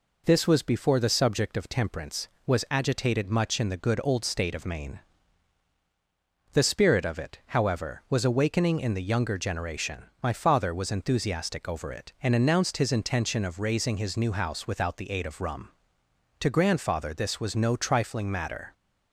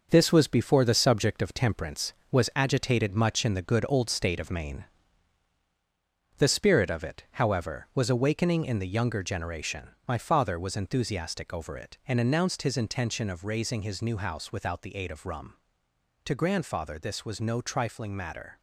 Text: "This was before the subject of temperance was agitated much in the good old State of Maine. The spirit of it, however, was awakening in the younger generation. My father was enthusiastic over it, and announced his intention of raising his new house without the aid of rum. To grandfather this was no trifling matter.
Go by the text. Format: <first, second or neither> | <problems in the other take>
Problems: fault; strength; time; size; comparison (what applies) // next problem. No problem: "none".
first | gets quieter; throughout; 6.5 dB